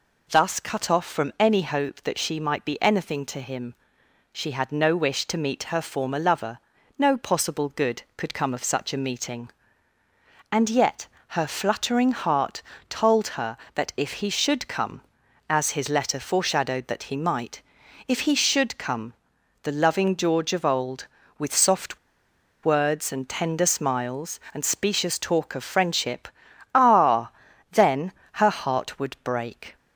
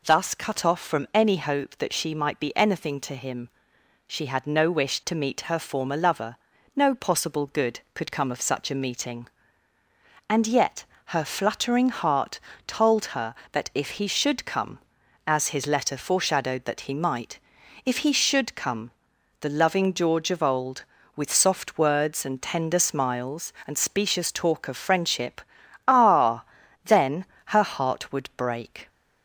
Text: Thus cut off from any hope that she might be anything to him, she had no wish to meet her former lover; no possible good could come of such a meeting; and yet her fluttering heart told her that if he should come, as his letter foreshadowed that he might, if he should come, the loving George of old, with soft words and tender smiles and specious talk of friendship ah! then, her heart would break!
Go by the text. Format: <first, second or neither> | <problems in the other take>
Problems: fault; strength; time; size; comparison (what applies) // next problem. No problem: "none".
second | pauses between "yet" and "her"; slight; at 11.0 s; 0.22 s long; slight in the second // pauses between "heart" and "told"; slight; at 12.6 s; 0.26 s long; slight in the second // pauses between "soft" and "words"; noticeable; at 21.9 s; 0.67 s long // pauses between "friendship" and "ah"; noticeable; at 26.2 s; 0.46 s long; noticeable in the second